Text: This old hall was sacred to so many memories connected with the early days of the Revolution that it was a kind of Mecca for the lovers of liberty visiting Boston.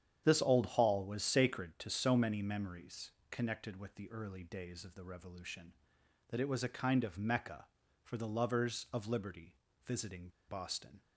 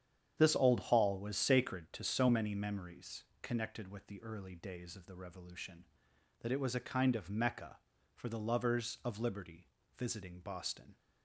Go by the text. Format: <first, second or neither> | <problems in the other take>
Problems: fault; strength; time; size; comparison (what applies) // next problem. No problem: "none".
second | starts louder than the rest; strong; until 1.2 s; 9 dB; strong in the second // pauses between "memories" and "connected"; slight; at 3.1 s; 0.18 s long; slight in the second // pauses between "liberty" and "visiting"; slight; at 9.5 s; 0.30 s long; slight in the second // pauses between "visiting" and "Boston"; slight; at 10.2 s; 0.19 s long